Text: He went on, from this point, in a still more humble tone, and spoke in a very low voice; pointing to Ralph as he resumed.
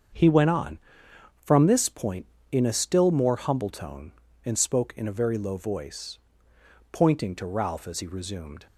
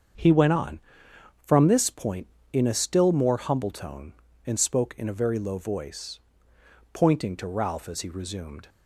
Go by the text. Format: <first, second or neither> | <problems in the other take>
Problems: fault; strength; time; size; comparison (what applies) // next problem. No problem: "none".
neither | starts louder than the rest; strong; the same in both